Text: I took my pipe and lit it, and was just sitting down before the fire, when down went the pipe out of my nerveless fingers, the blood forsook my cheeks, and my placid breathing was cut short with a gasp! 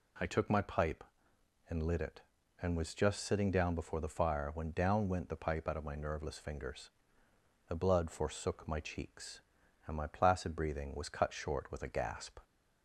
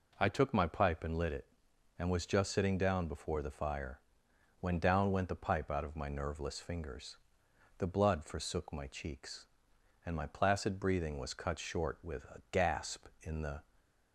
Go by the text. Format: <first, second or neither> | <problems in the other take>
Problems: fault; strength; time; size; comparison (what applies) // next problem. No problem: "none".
first | goes on to say "In the"; slight; from 13.2 s on; 0.42 s long